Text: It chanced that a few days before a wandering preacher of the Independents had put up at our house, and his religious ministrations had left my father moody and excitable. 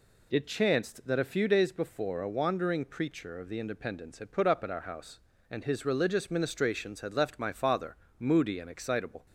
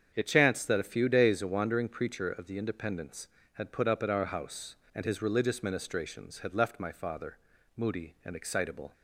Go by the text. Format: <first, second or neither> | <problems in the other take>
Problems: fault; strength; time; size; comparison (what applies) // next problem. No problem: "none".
first | starts louder than the rest; strong; until 1.1 s; 7.5 dB // skips "before"; at 1.4 s // pauses between "father" and "moody"; at 7.3 s; 0.40 s long; slight in the first